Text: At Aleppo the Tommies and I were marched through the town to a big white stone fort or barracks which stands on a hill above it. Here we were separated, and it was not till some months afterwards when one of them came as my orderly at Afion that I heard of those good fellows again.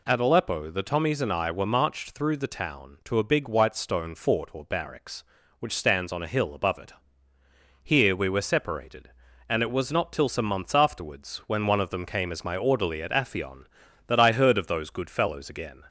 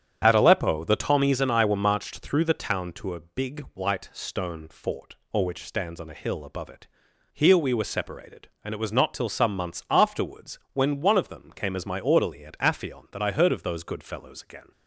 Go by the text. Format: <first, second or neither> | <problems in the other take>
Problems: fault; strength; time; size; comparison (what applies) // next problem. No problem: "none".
first | starts louder than the rest; strong; until 1.2 s; 8.5 dB // skips "barracks"; at 5.4 s